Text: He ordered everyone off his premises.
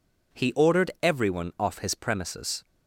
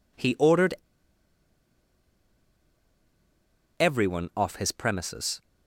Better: first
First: none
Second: pauses between "ordered" and "everyone"; strong; at 0.7 s; 3.0 s long

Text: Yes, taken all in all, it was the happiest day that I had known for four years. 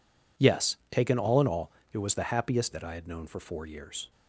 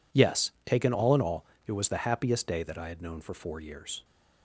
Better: second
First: skips "day"; at 2.7 s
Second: none

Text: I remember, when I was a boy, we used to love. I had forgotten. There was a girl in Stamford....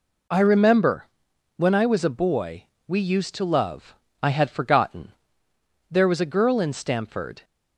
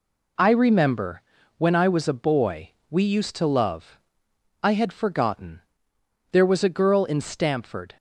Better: neither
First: none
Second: none

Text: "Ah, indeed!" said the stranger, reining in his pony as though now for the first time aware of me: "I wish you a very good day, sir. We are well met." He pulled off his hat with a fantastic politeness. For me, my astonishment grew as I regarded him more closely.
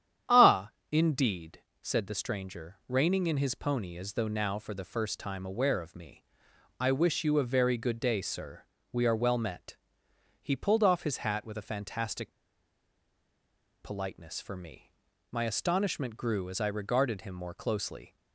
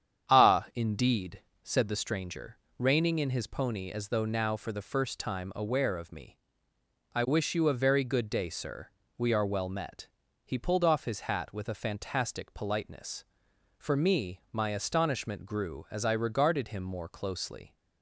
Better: second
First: starts louder than the rest; strong; until 1.5 s; 9.5 dB // pauses between "fantastic" and "politeness"; strong; at 12.3 s; 1.5 s long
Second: starts louder than the rest; strong; until 1.4 s; 8.5 dB

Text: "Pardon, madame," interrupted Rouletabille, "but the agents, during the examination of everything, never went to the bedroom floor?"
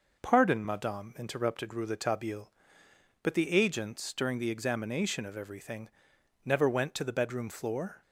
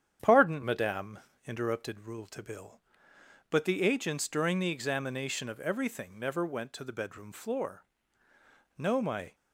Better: first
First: none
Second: starts louder than the rest; strong; until 1.4 s; 9 dB // goes on to say "No my"; from 8.7 s on; 0.58 s long

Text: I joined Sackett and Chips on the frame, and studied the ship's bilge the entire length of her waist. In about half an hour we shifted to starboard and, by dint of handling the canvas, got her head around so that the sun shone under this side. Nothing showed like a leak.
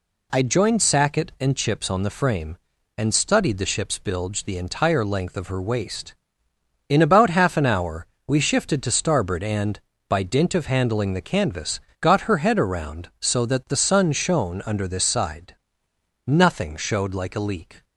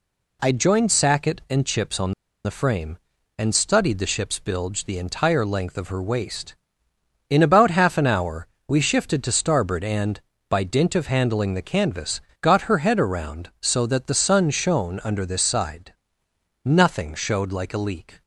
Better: first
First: pauses between "hour" and "we"; slight; at 8.0 s; 0.20 s long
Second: pauses between "on" and "the"; slight; at 2.1 s; 0.32 s long // pauses between "hour" and "we"; slight; at 8.4 s; 0.20 s long

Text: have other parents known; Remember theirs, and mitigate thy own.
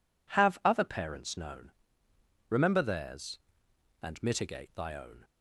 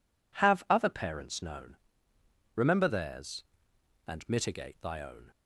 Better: neither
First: none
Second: none

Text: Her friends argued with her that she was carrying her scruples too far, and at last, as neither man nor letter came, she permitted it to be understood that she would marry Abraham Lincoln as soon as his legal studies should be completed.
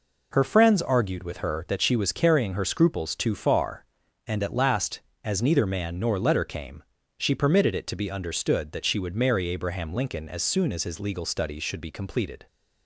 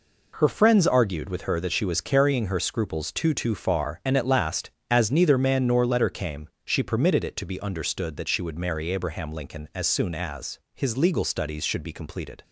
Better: first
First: none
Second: says "too" twice; at 3.3 s

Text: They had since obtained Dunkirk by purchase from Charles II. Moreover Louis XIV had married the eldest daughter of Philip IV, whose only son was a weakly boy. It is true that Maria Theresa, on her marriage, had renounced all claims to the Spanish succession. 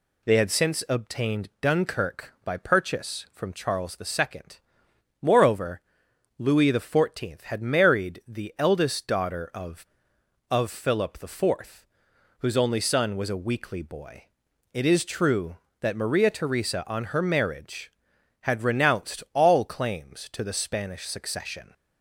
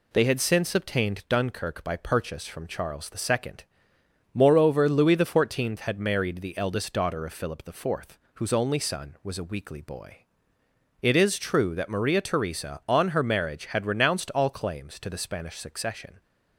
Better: second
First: pauses between "Moreover" and "Louis"; noticeable; at 5.8 s; 0.56 s long // says "of" twice; at 10.5 s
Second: none

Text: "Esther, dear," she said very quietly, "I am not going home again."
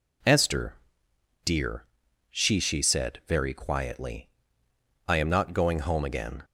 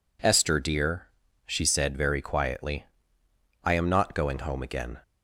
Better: second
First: says "she" twice; at 2.5 s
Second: none

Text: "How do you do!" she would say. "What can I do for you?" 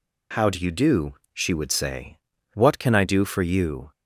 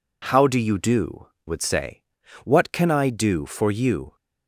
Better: first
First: none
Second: skips "she"; at 1.3 s

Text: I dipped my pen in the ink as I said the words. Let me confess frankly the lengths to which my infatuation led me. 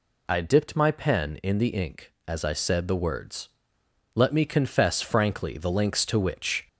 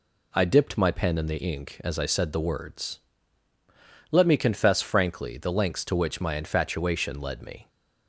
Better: second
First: stops before "my infatuation led me"; at 6.6 s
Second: none

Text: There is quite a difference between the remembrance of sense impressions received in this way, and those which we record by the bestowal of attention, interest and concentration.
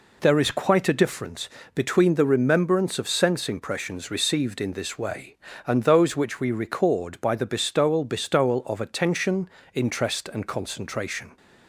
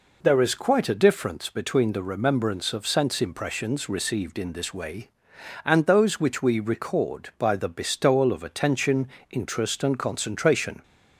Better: second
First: pauses between "difference" and "between"; slight; at 1.4 s; 0.26 s long // says "bestowal" twice; at 8.0 s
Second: none

